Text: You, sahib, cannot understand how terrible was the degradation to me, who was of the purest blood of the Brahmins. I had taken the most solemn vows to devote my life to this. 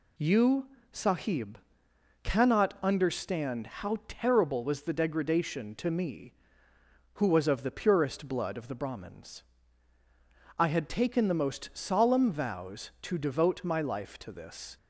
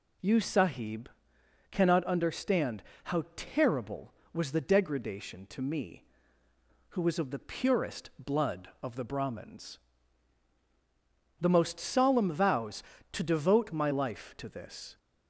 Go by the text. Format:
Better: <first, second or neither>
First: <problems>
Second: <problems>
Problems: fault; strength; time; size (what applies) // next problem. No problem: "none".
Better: first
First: none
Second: pauses between "understand" and "how"; slight; at 2.8 s; 0.22 s long // skips "I had taken"; at 10.5 s